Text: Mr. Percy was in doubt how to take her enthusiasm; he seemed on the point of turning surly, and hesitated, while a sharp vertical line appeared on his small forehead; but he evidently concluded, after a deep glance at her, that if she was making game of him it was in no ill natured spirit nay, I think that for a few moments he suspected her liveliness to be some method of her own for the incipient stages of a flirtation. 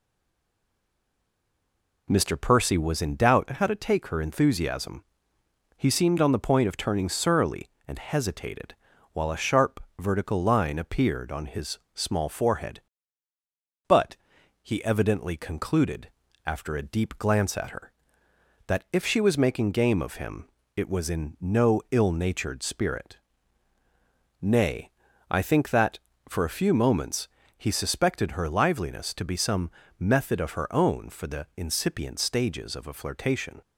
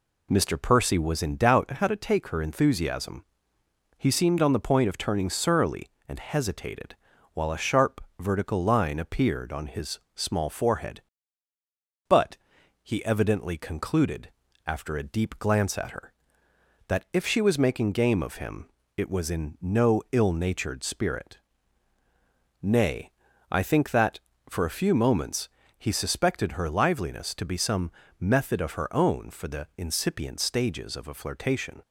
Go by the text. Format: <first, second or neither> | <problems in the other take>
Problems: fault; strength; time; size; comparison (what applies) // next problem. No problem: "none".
second | stays silent before the first word; noticeable; until 2.0 s; 2.0 s long // pauses between "sharp" and "vertical"; slight; at 9.7 s; 0.20 s long; slight in the second // pauses between "his" and "small"; slight; at 11.7 s; 0.16 s long; slight in the second // pauses between "but" and "he"; noticeable; at 14.1 s; 0.46 s long; noticeable in the second // pauses between "him" and "it"; slight; at 20.4 s; 0.26 s long; slight in the second // pauses between "spirit" and "nay"; at 23.1 s; 1.2 s long; also in the second // pauses between "moments" and "he"; slight; at 27.2 s; 0.34 s long; slight in the second // pauses between "some" and "method"; slight; at 29.6 s; 0.30 s long; slight in the second